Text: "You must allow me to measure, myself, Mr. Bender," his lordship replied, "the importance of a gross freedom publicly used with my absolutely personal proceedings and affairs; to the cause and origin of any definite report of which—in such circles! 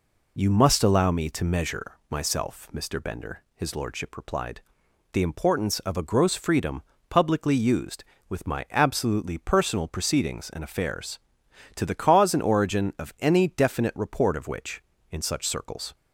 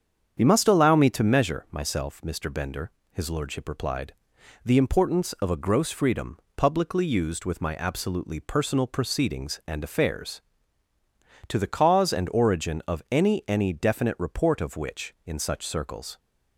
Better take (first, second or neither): first